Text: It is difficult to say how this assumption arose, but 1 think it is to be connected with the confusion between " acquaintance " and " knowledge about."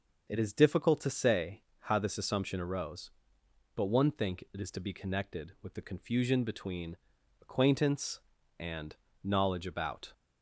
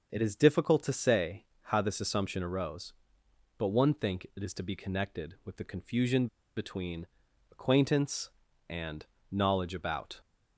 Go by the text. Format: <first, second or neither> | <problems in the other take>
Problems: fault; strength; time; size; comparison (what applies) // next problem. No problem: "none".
first | starts louder than the rest; until 1.1 s; 6.5 dB; also in the first // pauses between "say" and "how"; slight; at 1.4 s; 0.18 s long; slight in the first // pauses between "confusion" and "between"; slight; at 6.2 s; 0.29 s long